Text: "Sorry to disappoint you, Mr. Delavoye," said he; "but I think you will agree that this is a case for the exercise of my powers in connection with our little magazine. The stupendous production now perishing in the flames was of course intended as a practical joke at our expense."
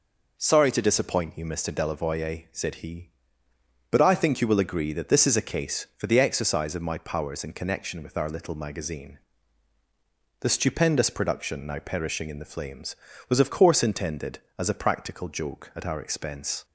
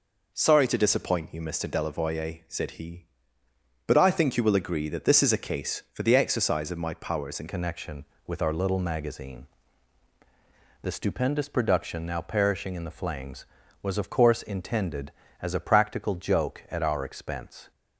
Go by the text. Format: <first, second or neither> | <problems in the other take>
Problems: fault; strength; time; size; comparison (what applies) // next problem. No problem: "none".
first | changes voice at "connection"; from 7.4 s on; 10.3 s long